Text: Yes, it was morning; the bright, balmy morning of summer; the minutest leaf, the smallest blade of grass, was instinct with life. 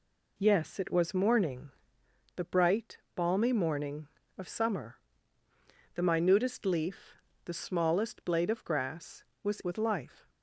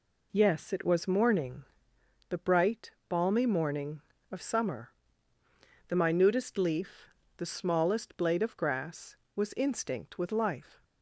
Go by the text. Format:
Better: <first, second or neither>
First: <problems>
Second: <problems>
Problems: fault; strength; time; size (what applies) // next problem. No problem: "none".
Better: second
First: skips "instinct"; at 9.6 s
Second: none